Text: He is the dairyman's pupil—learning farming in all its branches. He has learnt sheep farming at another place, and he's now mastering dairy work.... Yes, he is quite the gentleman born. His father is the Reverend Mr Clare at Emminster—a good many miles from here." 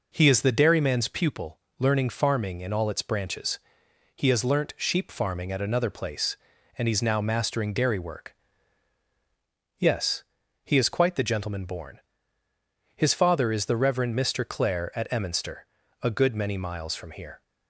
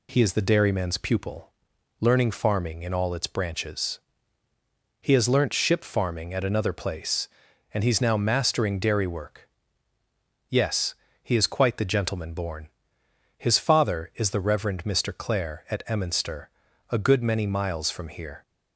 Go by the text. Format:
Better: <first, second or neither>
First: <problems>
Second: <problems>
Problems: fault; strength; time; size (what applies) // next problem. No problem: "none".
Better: first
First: none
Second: says "ship" for "sheep"; at 5.5 s